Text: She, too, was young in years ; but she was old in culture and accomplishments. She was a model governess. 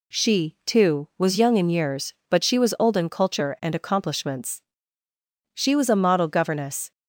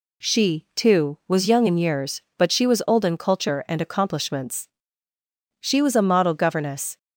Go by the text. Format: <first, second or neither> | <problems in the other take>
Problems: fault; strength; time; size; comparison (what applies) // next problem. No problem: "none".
neither | none